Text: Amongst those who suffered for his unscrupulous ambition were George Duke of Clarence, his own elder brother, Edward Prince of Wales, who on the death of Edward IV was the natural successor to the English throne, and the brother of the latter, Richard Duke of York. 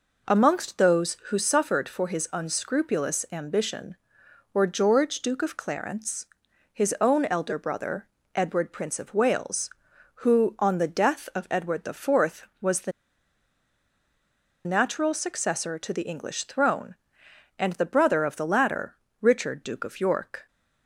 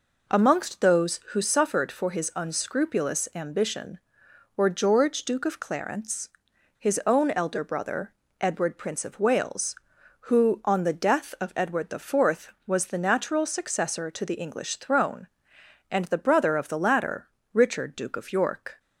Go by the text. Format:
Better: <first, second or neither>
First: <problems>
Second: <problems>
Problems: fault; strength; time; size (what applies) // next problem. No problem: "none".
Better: second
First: pauses between "the" and "natural"; strong; at 12.9 s; 1.7 s long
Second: none